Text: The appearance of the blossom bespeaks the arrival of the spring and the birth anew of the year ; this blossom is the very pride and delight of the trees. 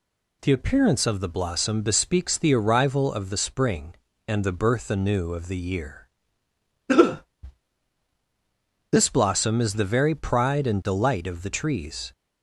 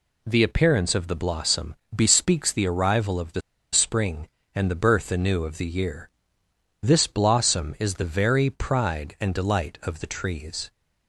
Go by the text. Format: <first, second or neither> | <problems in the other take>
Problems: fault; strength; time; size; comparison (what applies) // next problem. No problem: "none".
first | pauses between "blossom" and "bespeaks"; slight; at 1.7 s; 0.20 s long // pauses between "the" and "spring"; slight; at 3.4 s; 0.32 s long